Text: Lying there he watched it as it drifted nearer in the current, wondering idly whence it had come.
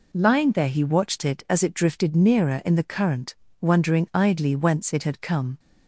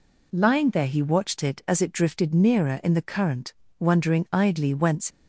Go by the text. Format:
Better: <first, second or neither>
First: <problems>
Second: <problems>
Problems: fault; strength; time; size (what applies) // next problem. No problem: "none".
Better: first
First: none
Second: stops before "it had come"; at 5.1 s